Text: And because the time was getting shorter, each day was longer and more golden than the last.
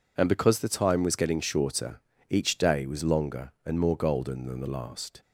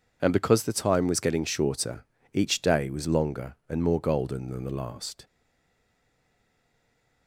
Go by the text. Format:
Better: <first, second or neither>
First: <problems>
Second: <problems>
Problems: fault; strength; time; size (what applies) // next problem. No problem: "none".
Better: first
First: none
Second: stays silent after the last word; noticeable; from 5.2 s on; 2.0 s long